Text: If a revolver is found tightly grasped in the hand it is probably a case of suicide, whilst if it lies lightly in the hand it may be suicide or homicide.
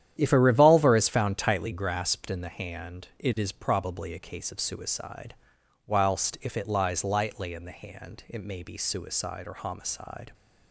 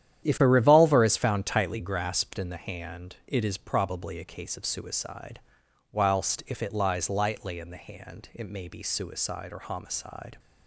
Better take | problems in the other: neither | starts louder than the rest; strong; the same in both

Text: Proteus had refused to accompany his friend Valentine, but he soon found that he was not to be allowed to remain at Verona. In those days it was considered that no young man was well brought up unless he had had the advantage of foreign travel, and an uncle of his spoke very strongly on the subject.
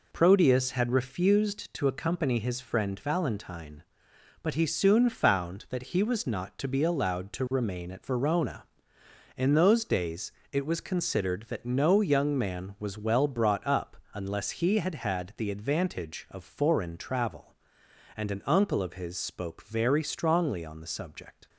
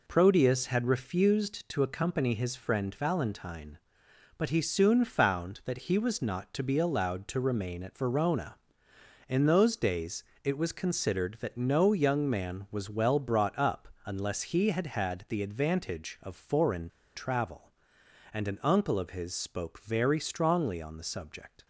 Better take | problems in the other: first | pauses between "days" and "it"; slight; at 10.2 s; 0.22 s long; slight in the first // pauses between "up" and "unless"; slight; at 13.8 s; 0.16 s long; slight in the first // pauses between "foreign" and "travel"; slight; at 16.8 s; 0.26 s long

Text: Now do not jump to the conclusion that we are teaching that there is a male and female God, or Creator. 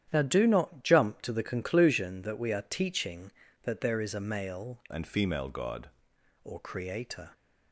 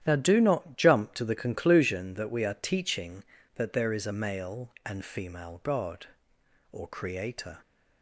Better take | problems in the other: second | starts louder than the rest; strong; until 1.1 s; 10.5 dB; strong in the second // changes voice from "and" to "God"; from 4.9 to 5.8 s; 0.9 s long

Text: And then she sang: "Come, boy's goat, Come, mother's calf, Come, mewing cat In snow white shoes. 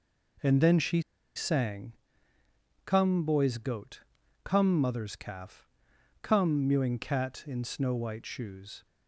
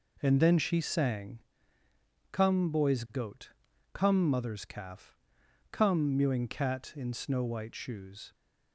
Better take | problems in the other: second | pauses between "she" and "sang"; slight; at 1.0 s; 0.35 s long

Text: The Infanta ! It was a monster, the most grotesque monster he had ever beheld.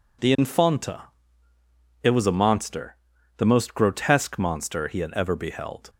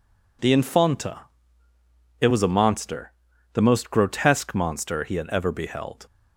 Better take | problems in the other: neither | none

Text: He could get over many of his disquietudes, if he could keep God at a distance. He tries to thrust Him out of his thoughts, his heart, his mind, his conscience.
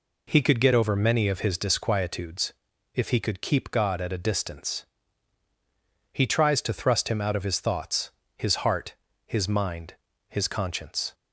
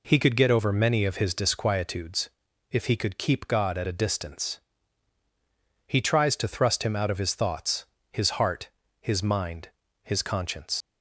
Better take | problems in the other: first | leaves "conscience" unfinished; at 10.8 s; 80 ms

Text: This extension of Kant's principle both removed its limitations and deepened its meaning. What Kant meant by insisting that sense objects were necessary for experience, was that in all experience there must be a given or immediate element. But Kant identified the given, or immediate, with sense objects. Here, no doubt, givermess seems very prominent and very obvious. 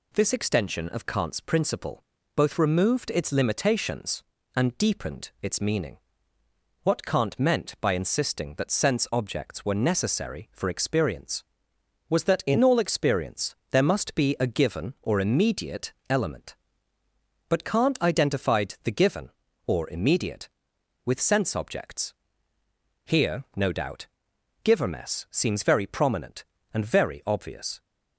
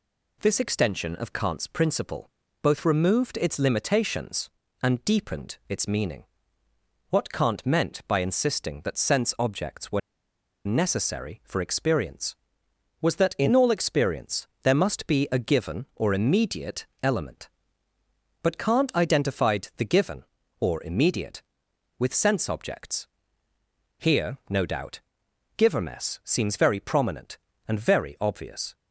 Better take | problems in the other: first | pauses between "principle" and "both"; slight; at 2.3 s; 0.32 s long; slight in the first // pauses between "were" and "necessary"; noticeable; at 10.0 s; 0.65 s long // pauses between "immediate" and "element"; slight; at 16.8 s; 0.16 s long; slight in the first

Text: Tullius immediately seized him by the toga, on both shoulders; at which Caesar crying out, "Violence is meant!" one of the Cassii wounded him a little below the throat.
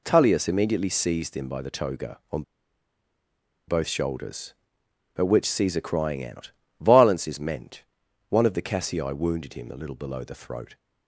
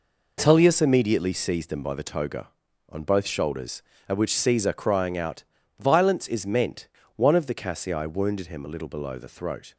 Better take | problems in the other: second | pauses between "on" and "both"; strong; at 2.4 s; 1.2 s long

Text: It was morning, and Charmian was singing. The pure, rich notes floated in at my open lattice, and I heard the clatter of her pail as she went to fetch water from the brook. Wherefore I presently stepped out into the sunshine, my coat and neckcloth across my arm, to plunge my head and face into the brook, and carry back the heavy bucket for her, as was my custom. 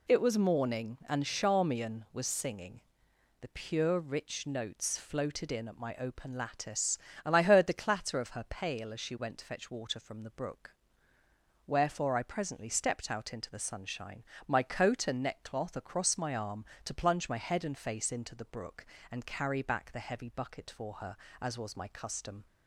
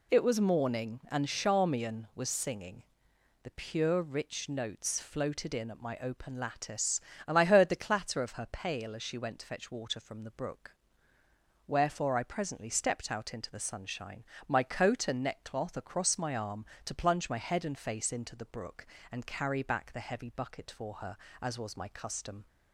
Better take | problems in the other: neither | none

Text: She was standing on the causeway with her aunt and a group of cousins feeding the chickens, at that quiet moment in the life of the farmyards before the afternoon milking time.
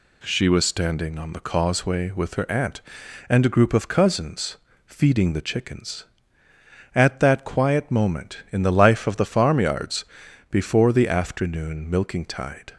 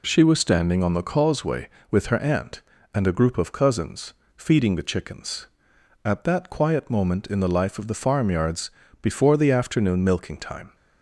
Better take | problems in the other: second | pauses between "cousins" and "feeding"; slight; at 4.5 s; 0.30 s long; slight in the second // pauses between "farmyards" and "before"; noticeable; at 10.0 s; 0.46 s long; slight in the second // says "tide" for "time"; at 12.2 s

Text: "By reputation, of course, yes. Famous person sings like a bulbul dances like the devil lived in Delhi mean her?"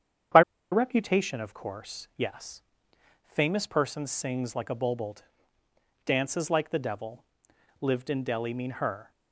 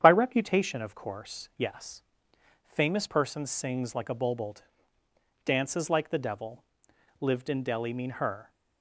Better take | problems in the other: second | starts louder than the rest; strong; until 1.6 s; 8.5 dB; strong in the second // pauses between "By" and "reputation"; slight; at 0.4 s; 0.31 s long // pauses between "bulbul" and "dances"; noticeable; at 5.1 s; 0.88 s long; noticeable in the second // pauses between "devil" and "lived"; noticeable; at 7.2 s; 0.56 s long; noticeable in the second

